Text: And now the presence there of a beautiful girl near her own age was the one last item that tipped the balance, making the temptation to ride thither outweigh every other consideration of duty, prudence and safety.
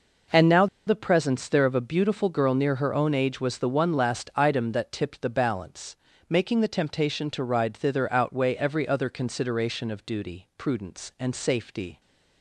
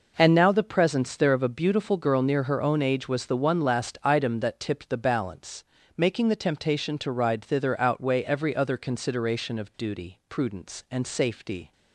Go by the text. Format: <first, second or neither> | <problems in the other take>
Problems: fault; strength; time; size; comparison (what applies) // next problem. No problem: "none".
second | pauses between "now" and "the"; slight; at 0.6 s; 0.20 s long